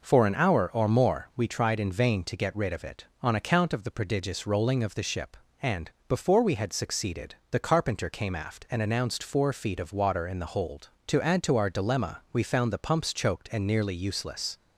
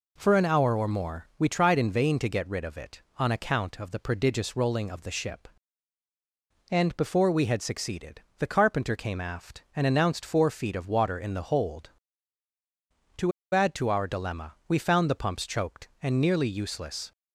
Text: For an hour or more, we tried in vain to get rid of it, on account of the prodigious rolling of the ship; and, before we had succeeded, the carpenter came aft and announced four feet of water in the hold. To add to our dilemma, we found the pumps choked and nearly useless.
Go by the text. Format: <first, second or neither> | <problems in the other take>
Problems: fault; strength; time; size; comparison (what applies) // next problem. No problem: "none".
first | pauses between "To" and "add"; slight; at 13.3 s; 0.22 s long